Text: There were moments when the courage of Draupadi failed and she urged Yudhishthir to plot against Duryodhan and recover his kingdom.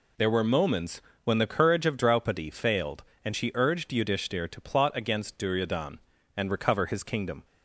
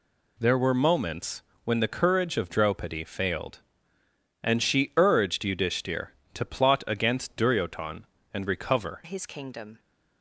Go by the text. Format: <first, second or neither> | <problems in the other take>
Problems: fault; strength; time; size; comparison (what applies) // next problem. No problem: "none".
first | pauses between "moments" and "when"; slight; at 1.4 s; 0.22 s long; slight in the first // changes voice at "his"; from 9.0 s on; 0.7 s long